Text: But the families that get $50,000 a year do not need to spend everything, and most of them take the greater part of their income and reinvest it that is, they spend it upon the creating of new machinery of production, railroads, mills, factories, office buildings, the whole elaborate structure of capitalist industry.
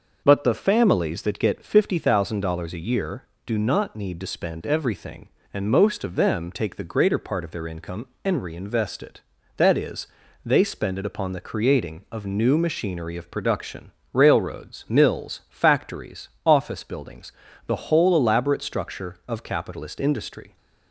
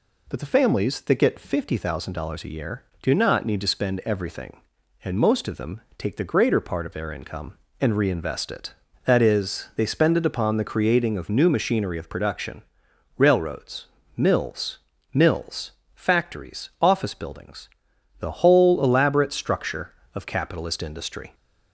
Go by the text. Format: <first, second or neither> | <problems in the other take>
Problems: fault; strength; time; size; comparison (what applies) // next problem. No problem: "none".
first | pauses between "them" and "take"; slight; at 5.8 s; 0.16 s long // says "mills" twice; at 15.1 s